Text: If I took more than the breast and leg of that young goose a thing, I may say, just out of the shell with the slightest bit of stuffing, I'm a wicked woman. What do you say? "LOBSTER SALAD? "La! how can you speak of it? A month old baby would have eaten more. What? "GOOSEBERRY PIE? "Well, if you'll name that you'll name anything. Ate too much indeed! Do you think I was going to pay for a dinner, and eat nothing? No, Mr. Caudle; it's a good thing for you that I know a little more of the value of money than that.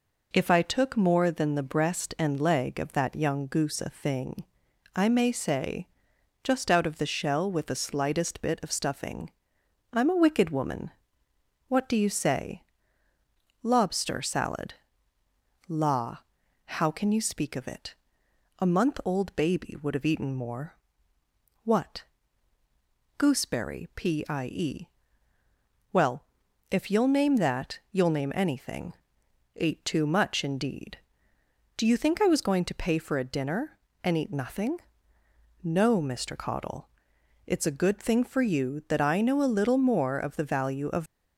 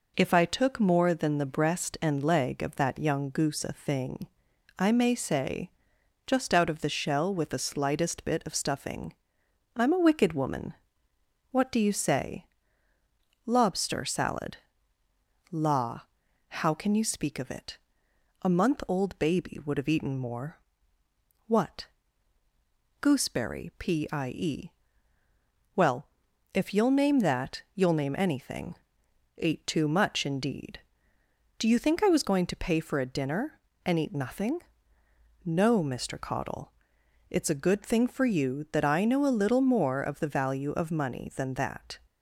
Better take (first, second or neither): second